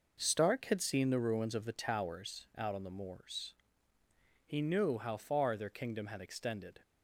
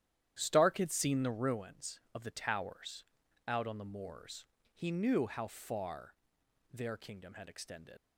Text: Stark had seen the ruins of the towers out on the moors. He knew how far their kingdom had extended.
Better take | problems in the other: first | starts louder than the rest; strong; until 1.4 s; 11 dB // pauses between "towers" and "out"; at 3.0 s; 0.44 s long // pauses between "far" and "their"; noticeable; at 6.1 s; 0.58 s long // leaves "extended" unfinished; at 7.9 s; 85 ms

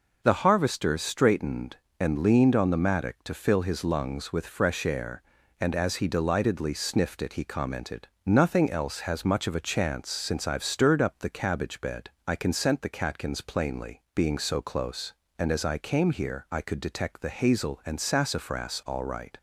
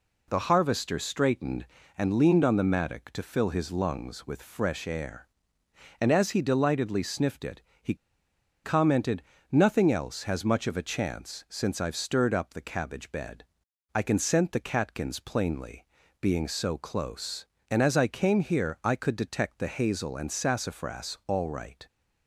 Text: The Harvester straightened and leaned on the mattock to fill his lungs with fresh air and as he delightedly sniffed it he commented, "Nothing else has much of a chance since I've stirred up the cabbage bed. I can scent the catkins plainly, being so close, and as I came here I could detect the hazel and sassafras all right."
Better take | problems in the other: first | pauses between "it" and "he"; slight; at 7.6 s; 0.20 s long // pauses between "he" and "commented"; noticeable; at 7.9 s; 0.69 s long

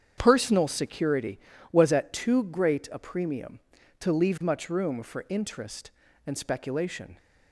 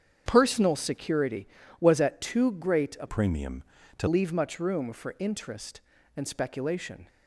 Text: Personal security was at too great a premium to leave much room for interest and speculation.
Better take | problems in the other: first | starts louder than the rest; strong; until 1.2 s; 8 dB; strong in the first // changes voice from "premium" to "to"; from 3.0 to 4.0 s; 1.0 s long

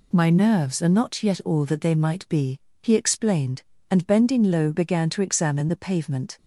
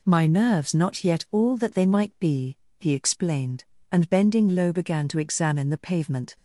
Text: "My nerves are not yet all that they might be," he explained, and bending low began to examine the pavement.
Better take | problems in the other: first | skips "are"; at 0.7 s

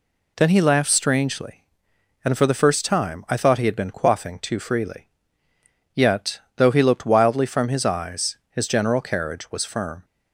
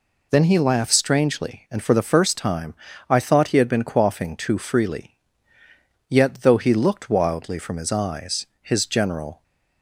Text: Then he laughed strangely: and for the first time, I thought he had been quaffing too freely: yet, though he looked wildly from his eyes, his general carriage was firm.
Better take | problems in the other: first | stops before "carriage was firm"; at 9.4 s

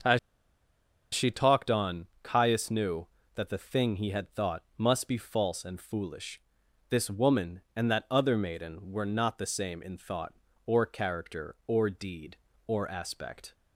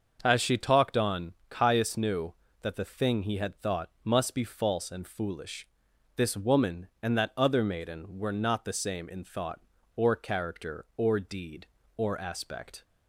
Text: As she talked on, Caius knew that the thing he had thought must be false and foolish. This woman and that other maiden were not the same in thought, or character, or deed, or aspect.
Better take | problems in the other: second | starts louder than the rest; until 1.9 s; 6 dB; also in the second // pauses between "As" and "she"; noticeable; at 0.1 s; 0.94 s long // pauses between "thought" and "must"; slight; at 4.6 s; 0.16 s long; slight in the second

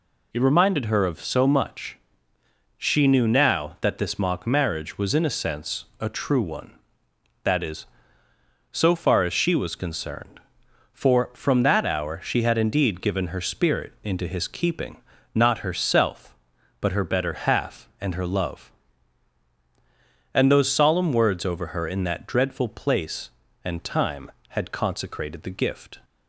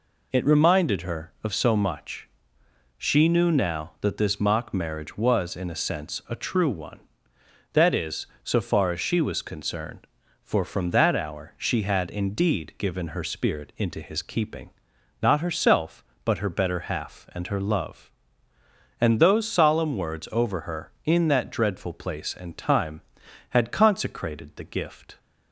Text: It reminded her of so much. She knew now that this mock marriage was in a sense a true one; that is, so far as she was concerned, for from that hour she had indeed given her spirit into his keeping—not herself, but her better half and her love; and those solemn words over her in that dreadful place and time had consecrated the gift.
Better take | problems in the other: neither | none

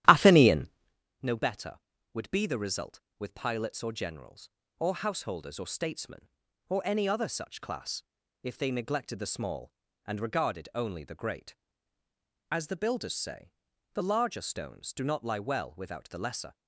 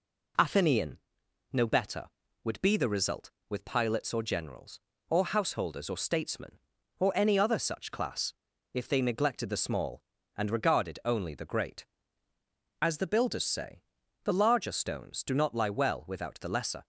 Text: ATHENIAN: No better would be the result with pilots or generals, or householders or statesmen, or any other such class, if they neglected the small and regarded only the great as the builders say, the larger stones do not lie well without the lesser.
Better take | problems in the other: second | starts louder than the rest; strong; until 1.0 s; 12.5 dB

